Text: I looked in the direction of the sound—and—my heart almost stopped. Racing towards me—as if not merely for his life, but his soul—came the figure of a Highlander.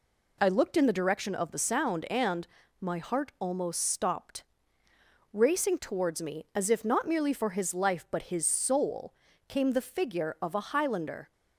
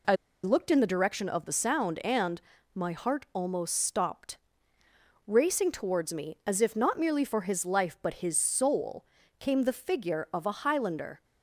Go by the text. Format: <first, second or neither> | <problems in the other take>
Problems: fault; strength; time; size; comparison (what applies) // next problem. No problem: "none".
first | pauses between "I" and "looked"; slight; at 0.1 s; 0.29 s long